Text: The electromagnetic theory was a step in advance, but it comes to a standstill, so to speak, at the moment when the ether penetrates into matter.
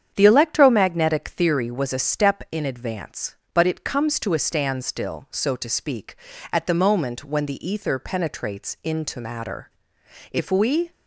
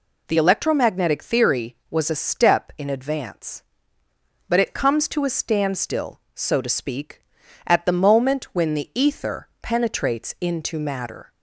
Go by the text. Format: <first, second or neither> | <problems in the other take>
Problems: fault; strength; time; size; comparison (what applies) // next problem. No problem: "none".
second | starts louder than the rest; strong; until 1.1 s; 8.5 dB // goes on to say "If we"; from 10.3 s on; 0.60 s long